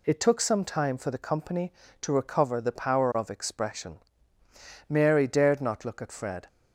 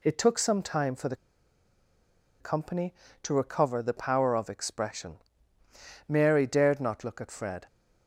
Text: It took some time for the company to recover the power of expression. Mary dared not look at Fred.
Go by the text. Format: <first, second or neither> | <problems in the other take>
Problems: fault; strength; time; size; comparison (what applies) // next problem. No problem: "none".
first | pauses between "the" and "company"; strong; at 1.1 s; 1.2 s long